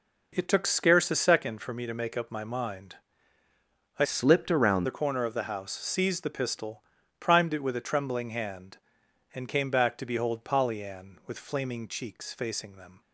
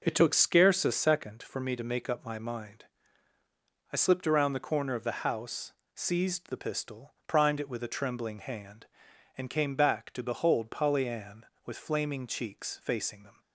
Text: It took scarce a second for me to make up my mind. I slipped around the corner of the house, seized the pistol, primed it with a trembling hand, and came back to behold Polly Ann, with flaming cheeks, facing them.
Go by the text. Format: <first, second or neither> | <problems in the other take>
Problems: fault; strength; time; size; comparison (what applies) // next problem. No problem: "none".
second | changes voice from "slipped" to "around"; from 4.0 to 4.8 s; 0.8 s long